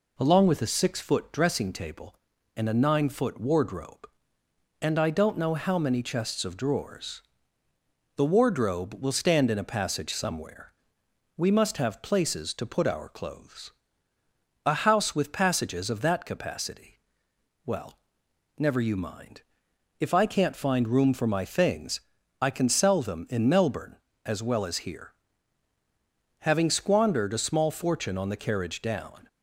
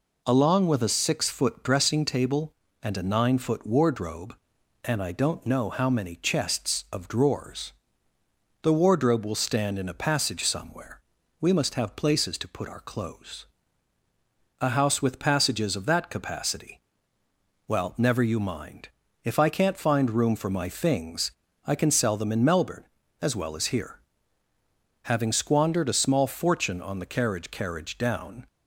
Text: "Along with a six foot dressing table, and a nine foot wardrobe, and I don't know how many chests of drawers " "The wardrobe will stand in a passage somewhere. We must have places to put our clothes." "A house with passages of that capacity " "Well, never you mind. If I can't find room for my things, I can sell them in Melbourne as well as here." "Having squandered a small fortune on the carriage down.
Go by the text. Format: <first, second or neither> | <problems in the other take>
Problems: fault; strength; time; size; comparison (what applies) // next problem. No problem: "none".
first | says "carriage" twice; at 27.5 s